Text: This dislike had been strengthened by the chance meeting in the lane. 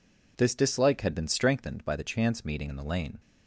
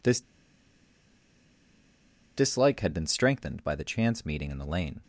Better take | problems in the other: first | pauses between "This" and "dislike"; strong; at 0.2 s; 2.1 s long

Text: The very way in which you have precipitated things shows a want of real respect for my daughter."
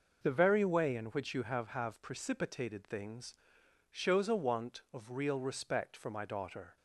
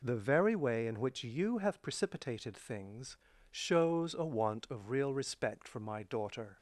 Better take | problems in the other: second | says "have" twice; at 1.7 s // pauses between "things" and "shows"; noticeable; at 3.3 s; 0.56 s long; also in the second

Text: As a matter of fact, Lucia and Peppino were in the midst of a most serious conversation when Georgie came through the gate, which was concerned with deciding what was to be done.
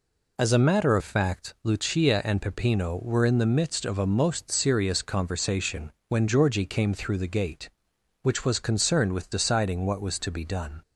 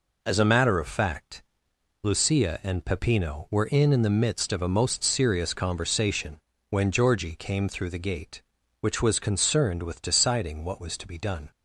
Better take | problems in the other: first | says "in" twice; at 3.9 s // pauses between "conversation" and "when"; slight; at 6.3 s; 0.30 s long; slight in the first

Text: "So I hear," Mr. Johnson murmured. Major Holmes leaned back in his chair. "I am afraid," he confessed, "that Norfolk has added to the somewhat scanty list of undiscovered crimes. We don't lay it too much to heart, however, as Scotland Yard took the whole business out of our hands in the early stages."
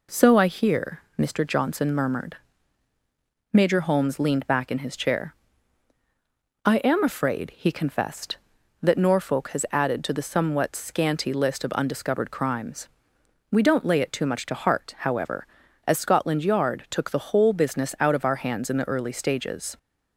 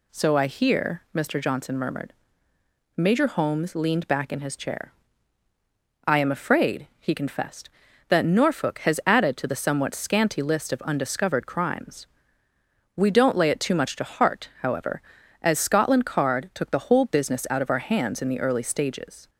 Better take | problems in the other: first | says "Card" for "Yard"; at 16.0 s

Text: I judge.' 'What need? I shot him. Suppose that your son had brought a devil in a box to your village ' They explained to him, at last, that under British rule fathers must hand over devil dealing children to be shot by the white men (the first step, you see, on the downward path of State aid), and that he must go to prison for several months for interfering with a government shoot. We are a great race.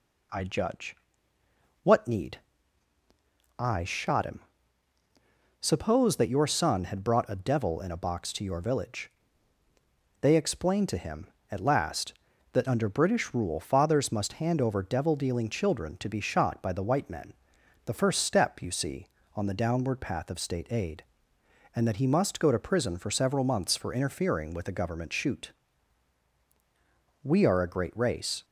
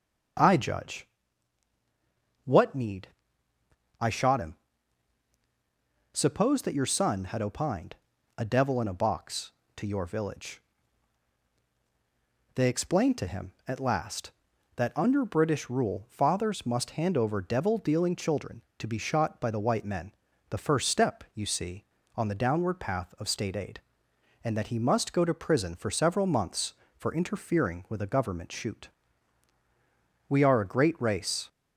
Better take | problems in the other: first | starts louder than the rest; strong; until 2.8 s; 8 dB // says "opined" for "brought"; at 7.4 s

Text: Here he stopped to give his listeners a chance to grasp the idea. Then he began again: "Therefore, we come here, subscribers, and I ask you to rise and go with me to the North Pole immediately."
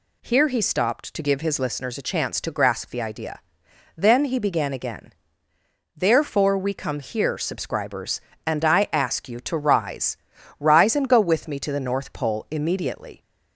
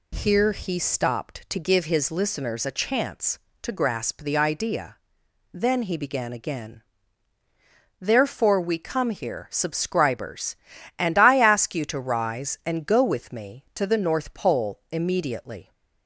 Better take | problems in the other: second | says "rise" twice; at 10.5 s

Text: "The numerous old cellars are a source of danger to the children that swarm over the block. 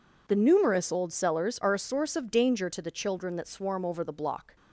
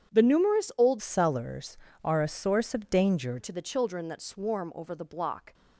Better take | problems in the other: first | starts louder than the rest; strong; until 1.1 s; 8.5 dB // changes voice from "cellars" to "danger"; from 0.9 to 3.3 s; 2.4 s long

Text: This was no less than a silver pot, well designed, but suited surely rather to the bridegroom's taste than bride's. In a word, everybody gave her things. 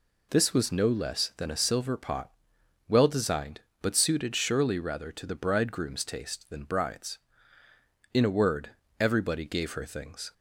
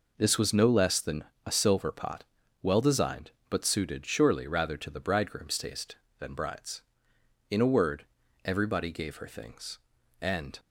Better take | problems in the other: first | pauses between "than" and "a"; slight; at 1.2 s; 0.20 s long // goes on to say "And"; slight; from 10.2 s on; 0.38 s long

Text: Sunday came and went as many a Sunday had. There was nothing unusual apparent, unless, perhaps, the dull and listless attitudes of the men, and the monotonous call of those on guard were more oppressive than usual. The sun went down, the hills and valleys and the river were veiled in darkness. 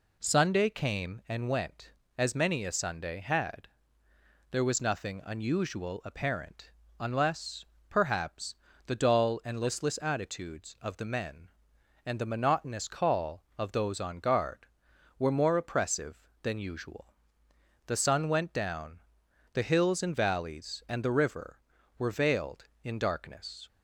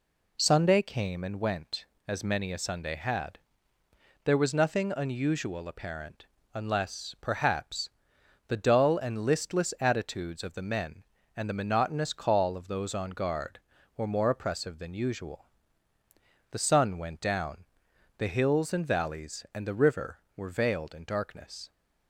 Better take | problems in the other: neither | none

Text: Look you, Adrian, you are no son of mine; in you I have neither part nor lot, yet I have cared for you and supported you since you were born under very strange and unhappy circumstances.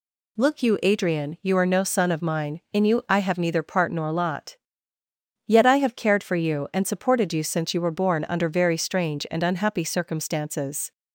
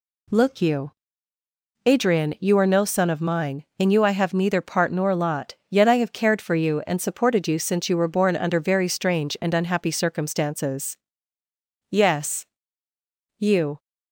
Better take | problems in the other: first | goes on to say "Yes you"; strong; from 11.8 s on; 1.9 s long

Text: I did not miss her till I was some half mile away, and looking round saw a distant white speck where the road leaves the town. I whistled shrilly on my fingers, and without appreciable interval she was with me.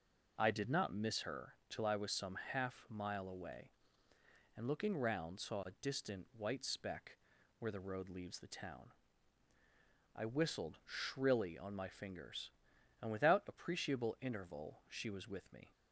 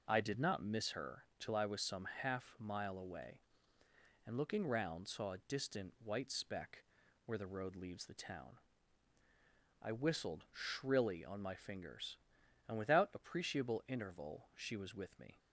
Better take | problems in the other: neither | pauses between "her" and "till"; slight; the same in both // pauses between "speck" and "where"; the same in both

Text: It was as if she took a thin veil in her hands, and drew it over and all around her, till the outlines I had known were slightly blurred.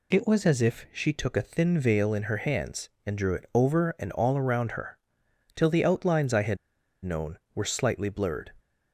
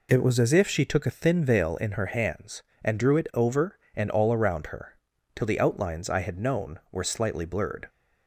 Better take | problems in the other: second | pauses between "had" and "known"; noticeable; at 6.5 s; 0.47 s long

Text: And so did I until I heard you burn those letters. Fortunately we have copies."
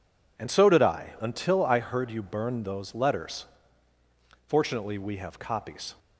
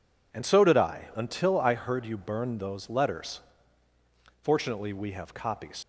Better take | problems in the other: first | leaves "copies" unfinished; at 5.8 s; 105 ms

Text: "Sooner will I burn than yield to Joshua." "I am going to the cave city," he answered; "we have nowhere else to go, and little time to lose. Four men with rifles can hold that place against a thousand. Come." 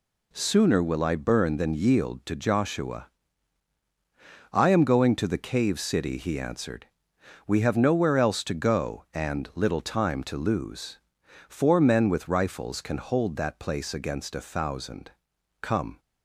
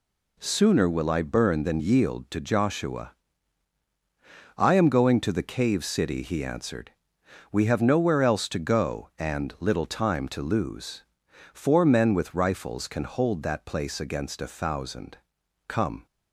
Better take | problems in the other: neither | none

